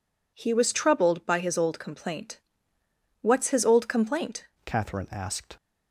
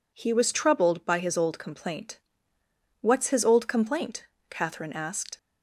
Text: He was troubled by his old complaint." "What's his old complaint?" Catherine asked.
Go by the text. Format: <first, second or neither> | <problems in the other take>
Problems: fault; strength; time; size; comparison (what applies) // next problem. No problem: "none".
second | changes voice at "Catherine"; from 4.6 s on; 0.9 s long